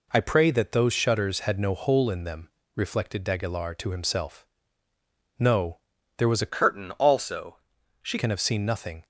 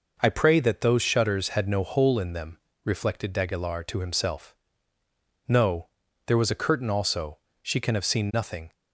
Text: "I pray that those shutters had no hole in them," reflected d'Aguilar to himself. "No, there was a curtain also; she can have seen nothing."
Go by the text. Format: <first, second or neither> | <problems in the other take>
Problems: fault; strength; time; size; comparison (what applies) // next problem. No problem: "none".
second | changes voice from "curtain" to "she"; from 6.4 to 8.1 s; 1.7 s long